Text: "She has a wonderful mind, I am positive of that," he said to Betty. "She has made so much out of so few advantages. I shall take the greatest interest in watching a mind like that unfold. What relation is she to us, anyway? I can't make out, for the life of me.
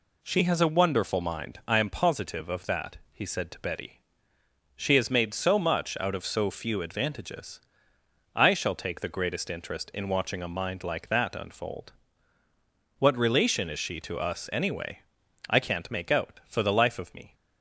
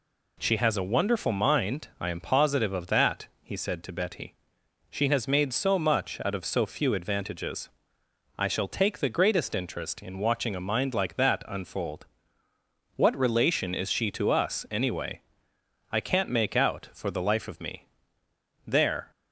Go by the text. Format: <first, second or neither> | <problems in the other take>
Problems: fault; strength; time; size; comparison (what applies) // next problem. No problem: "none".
first | goes on to say "There"; slight; from 18.6 s on; 0.46 s long